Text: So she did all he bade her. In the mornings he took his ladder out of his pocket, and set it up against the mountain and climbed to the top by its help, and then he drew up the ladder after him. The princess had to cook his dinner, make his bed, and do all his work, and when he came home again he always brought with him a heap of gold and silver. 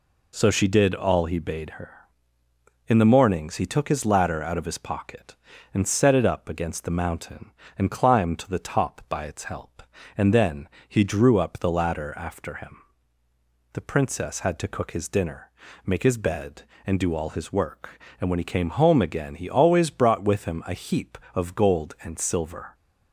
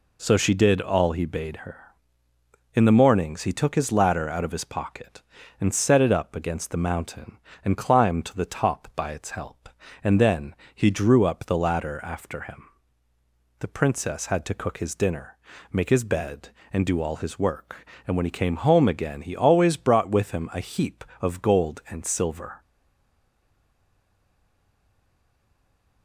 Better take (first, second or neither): first